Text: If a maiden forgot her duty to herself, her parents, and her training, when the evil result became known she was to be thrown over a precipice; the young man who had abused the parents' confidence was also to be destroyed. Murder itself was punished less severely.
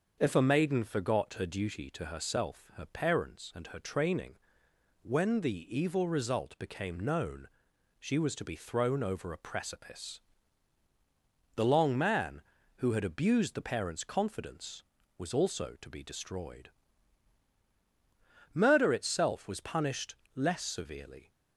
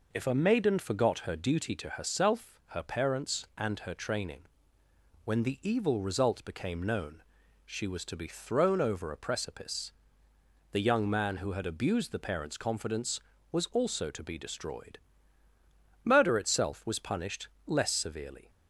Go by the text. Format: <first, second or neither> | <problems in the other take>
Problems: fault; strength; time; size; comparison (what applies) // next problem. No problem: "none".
second | starts louder than the rest; until 1.2 s; 6.5 dB // pauses between "known" and "she"; noticeable; at 7.4 s; 0.50 s long; also in the second // says "long" for "young"; at 11.6 s // pauses between "punished" and "less"; slight; at 20.1 s; 0.20 s long; slight in the second